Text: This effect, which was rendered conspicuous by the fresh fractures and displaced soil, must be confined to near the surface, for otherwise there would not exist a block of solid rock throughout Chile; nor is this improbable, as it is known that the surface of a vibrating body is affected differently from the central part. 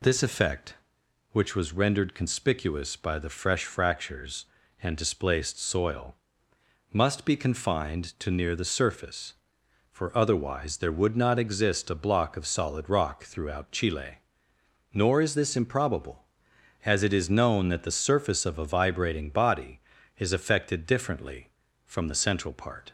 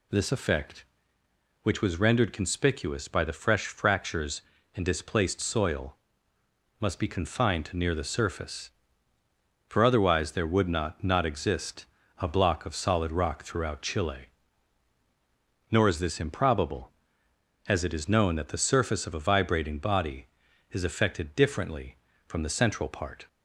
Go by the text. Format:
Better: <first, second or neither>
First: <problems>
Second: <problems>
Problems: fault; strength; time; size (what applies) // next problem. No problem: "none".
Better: first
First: none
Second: says "not" twice; at 11.0 s // pauses between "exist" and "a"; slight; at 11.8 s; 0.34 s long